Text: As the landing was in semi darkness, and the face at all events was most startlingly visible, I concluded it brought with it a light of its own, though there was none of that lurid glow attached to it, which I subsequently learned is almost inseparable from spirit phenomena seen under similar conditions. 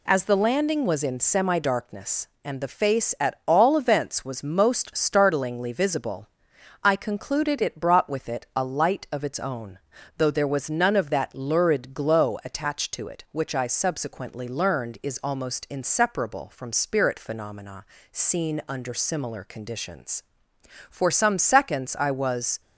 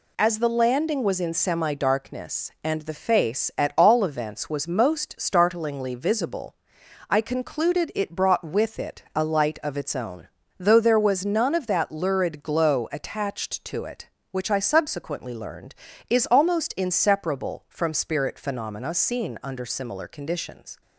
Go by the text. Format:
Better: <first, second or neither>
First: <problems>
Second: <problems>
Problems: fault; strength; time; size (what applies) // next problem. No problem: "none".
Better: second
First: pauses between "phenomena" and "seen"; slight; at 17.8 s; 0.28 s long // goes on to say "For some seconds I was"; strong; from 20.8 s on; 1.7 s long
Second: none